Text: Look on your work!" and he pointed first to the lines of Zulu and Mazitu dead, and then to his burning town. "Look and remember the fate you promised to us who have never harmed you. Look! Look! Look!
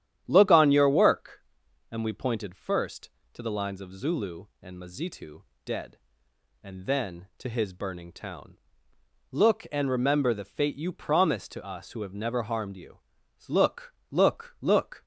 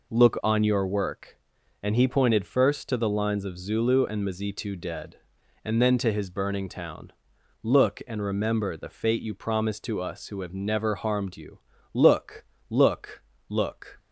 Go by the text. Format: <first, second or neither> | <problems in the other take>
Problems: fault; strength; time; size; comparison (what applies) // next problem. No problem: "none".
second | starts louder than the rest; strong; until 1.2 s; 10.5 dB // says "we" for "he"; at 2.0 s // pauses between "Mazitu" and "dead"; slight; at 5.4 s; 0.24 s long